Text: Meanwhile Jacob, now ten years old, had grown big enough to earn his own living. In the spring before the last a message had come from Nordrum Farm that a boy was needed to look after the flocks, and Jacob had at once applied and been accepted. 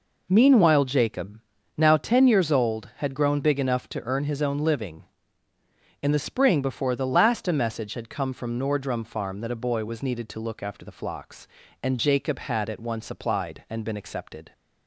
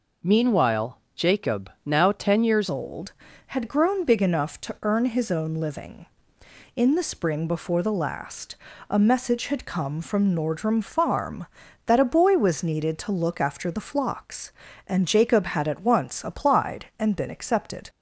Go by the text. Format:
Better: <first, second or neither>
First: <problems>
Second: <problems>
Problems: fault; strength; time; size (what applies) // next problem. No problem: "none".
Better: first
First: none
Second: pauses between "Meanwhile" and "Jacob"; slight; at 0.9 s; 0.18 s long // changes voice at "old"; from 2.6 s on; 15.2 s long // pauses between "last" and "a"; slight; at 8.5 s; 0.34 s long